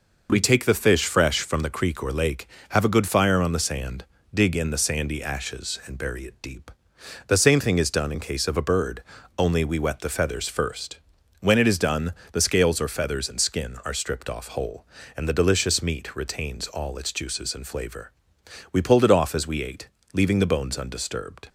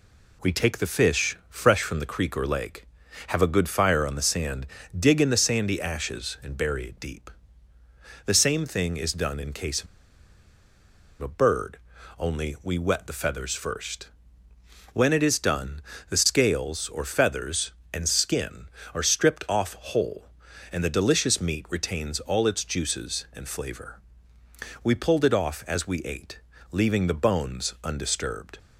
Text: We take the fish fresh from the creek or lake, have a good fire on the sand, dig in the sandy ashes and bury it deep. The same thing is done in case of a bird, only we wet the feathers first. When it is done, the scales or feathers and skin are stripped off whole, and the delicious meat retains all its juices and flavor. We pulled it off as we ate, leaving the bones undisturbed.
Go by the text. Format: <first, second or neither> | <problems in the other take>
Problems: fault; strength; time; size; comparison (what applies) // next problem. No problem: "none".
first | pauses between "of" and "a"; strong; at 9.8 s; 1.3 s long